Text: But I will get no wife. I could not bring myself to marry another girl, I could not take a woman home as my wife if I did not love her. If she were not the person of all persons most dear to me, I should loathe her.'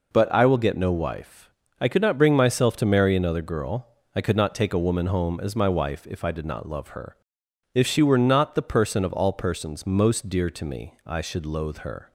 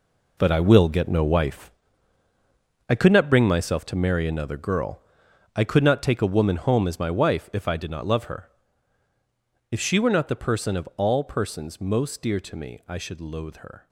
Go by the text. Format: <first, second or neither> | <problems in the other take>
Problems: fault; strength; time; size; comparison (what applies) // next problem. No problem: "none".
first | gets quieter; strong; throughout; 11.5 dB